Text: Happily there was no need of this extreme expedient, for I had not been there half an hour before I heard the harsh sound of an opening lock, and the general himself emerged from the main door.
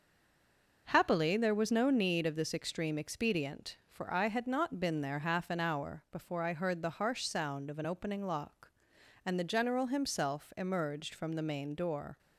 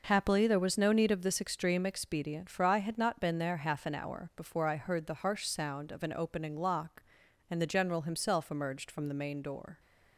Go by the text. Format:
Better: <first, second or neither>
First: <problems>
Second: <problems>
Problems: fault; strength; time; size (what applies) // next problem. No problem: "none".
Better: second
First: stays silent before the first word; slight; until 0.8 s; 0.8 s long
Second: none